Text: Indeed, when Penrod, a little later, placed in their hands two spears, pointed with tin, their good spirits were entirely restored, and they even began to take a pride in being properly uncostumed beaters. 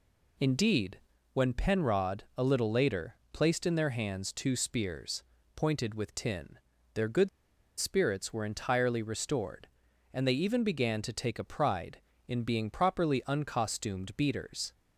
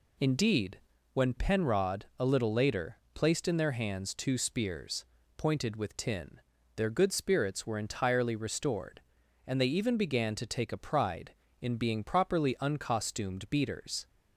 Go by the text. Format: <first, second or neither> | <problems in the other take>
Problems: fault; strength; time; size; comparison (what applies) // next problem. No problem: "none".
second | pauses between "good" and "spirits"; noticeable; at 7.2 s; 0.50 s long